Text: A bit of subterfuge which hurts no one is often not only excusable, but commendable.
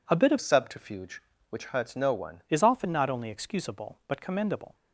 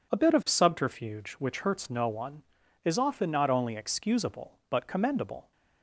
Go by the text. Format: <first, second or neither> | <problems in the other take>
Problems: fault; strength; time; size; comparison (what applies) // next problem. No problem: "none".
second | changes voice from "subterfuge" to "one"; from 0.3 to 2.4 s; 2.1 s long